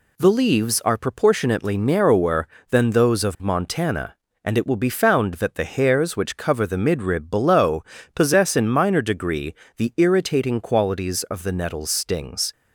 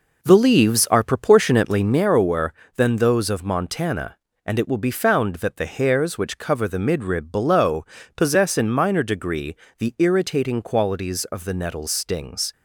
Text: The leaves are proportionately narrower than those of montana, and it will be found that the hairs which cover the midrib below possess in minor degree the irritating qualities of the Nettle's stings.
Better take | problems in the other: first | starts louder than the rest; noticeable; until 2.1 s; 4.5 dB // pauses between "below" and "possess"; slight; at 7.8 s; 0.30 s long; slight in the first // pauses between "degree" and "the"; slight; at 9.5 s; 0.24 s long; slight in the first

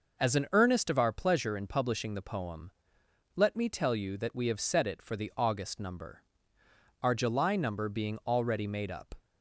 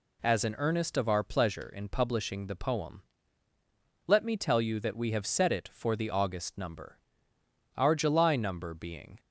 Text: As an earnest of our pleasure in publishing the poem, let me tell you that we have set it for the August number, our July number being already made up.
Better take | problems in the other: first | stops before "already made up"; at 9.1 s

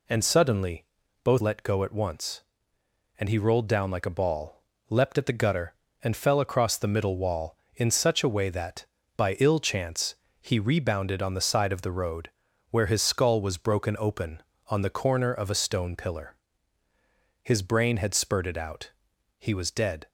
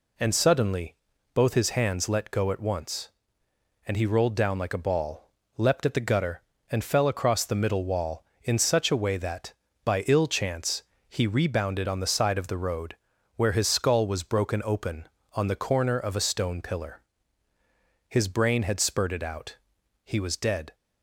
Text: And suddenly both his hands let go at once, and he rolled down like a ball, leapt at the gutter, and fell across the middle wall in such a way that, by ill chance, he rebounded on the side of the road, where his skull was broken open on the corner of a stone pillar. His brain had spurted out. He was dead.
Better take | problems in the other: second | pauses between "suddenly" and "both"; at 0.8 s; 0.38 s long; also in the second // skips "his hands"; at 1.4 s

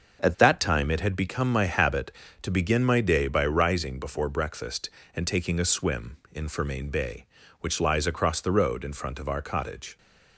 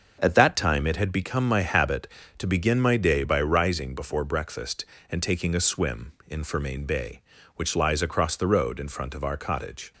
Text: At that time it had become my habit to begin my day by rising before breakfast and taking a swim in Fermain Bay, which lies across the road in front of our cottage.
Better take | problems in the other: neither | starts louder than the rest; the same in both

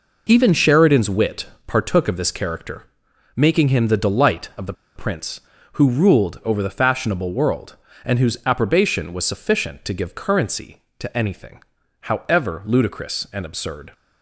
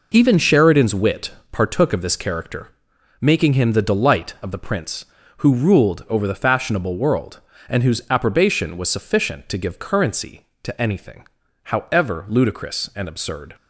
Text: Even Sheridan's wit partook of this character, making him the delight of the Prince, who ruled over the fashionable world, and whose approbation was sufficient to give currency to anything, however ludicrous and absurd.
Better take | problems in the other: second | pauses between "wit" and "partook"; slight; at 1.4 s; 0.20 s long; slight in the second // pauses between "the" and "Prince"; slight; at 4.7 s; 0.22 s long

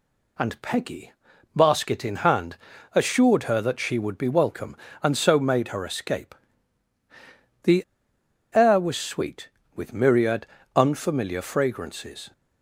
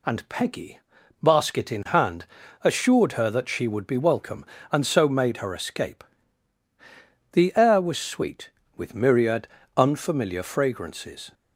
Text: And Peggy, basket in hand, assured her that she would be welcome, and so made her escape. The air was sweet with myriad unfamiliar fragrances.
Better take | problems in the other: second | pauses between "The" and "air"; noticeable; at 7.8 s; 0.69 s long // pauses between "myriad" and "unfamiliar"; slight; at 10.4 s; 0.28 s long; slight in the second

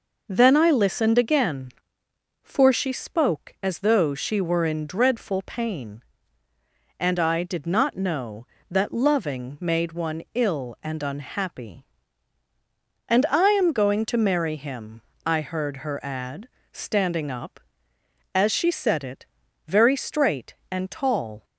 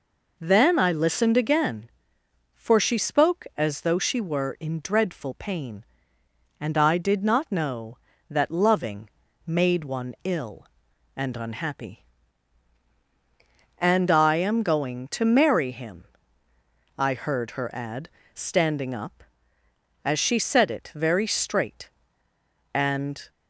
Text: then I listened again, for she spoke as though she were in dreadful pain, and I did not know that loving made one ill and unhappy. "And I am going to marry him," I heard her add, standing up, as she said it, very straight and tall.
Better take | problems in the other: first | pauses between "loving" and "made"; slight; at 9.0 s; 0.36 s long // stops before "tall"; at 23.2 s

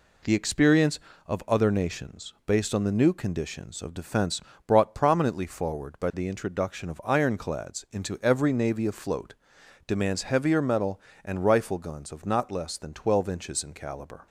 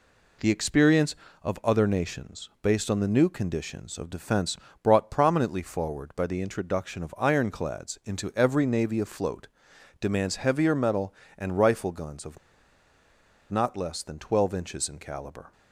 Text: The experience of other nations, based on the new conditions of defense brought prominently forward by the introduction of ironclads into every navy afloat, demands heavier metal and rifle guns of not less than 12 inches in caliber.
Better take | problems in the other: first | pauses between "defense" and "brought"; slight; at 4.5 s; 0.26 s long; slight in the first // pauses between "of" and "not"; at 12.3 s; 1.1 s long

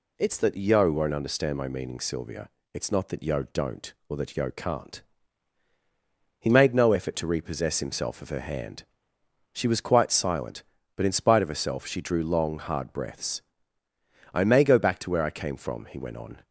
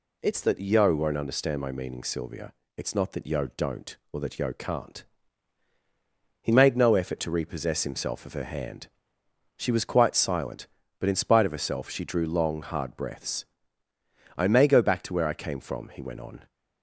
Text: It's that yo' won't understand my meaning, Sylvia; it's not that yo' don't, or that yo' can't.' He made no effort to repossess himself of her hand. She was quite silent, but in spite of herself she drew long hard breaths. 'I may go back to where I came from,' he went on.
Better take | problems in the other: neither | none

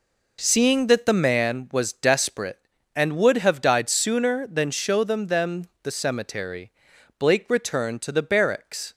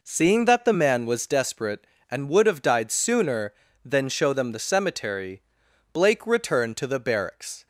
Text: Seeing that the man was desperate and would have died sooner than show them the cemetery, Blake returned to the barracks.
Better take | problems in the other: second | says "them" twice; at 5.2 s

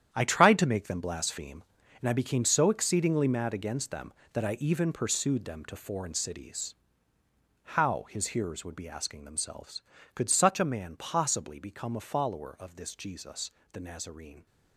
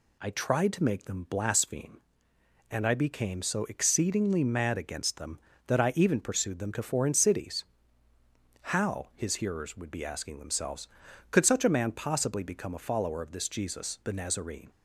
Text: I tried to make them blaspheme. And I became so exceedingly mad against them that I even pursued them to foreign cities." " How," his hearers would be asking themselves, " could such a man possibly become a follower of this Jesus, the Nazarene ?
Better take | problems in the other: second | gets quieter; strong; throughout; 12 dB

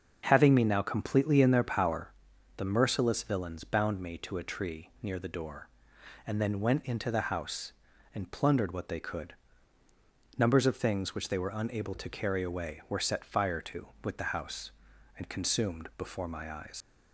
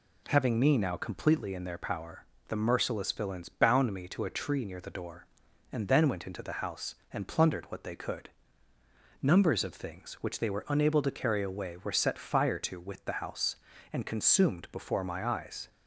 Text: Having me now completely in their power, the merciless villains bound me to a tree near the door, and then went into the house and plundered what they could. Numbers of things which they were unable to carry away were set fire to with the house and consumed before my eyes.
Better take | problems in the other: second | starts louder than the rest; until 1.2 s; 6.5 dB // leaves "eyes" unfinished; at 16.8 s; 100 ms

